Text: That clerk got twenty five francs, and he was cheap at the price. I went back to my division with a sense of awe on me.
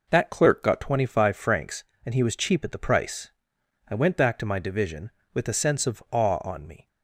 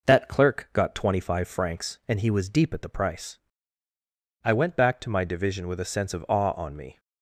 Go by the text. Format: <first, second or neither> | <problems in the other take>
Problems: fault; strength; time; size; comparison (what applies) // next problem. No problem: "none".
first | says "deep" for "cheap"; at 2.4 s